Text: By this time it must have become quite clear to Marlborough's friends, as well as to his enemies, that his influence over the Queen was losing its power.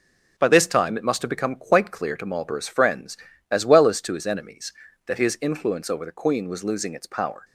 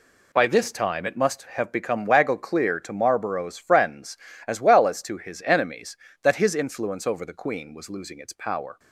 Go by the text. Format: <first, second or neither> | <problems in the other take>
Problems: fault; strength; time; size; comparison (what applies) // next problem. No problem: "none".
first | says "waggle" for "quite"; at 2.0 s